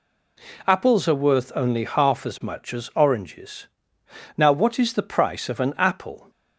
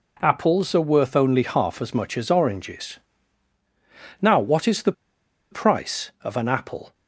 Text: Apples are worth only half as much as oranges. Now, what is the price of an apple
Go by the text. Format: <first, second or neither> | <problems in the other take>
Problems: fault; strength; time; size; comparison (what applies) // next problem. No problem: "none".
first | pauses between "the" and "price"; noticeable; at 4.9 s; 0.59 s long